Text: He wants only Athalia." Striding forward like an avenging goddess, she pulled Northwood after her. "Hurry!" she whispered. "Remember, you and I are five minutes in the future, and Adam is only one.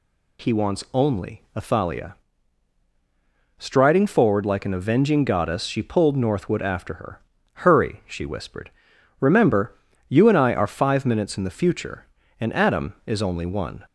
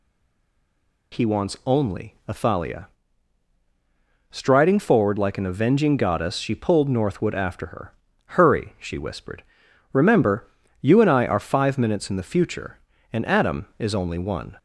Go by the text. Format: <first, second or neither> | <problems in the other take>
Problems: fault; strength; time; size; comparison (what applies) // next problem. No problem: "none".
first | stays silent before the first word; until 1.1 s; 1.1 s long